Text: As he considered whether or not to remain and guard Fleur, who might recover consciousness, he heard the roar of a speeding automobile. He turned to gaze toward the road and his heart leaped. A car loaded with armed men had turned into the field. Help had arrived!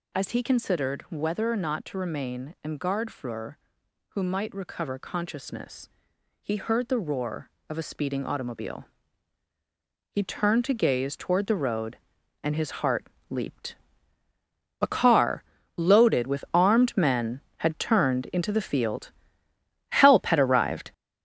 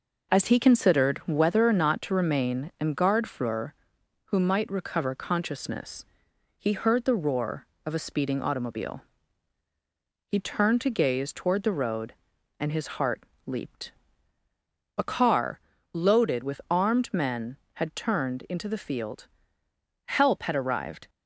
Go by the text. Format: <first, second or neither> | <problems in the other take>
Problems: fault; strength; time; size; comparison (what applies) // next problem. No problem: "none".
second | gets louder; throughout; 6.5 dB // pauses between "heart" and "leaped"; slight; at 13.0 s; 0.24 s long; slight in the second // pauses between "car" and "loaded"; slight; at 15.4 s; 0.36 s long; slight in the second